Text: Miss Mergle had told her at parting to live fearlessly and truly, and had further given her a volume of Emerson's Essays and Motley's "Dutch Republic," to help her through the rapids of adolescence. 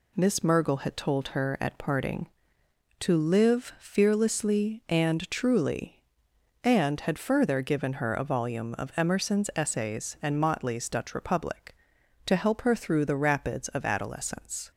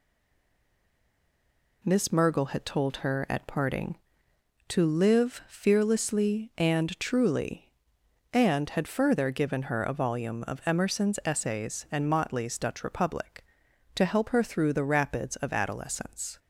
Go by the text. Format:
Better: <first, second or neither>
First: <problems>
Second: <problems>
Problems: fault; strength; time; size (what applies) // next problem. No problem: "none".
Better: first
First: none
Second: stays silent before the first word; noticeable; until 1.8 s; 1.8 s long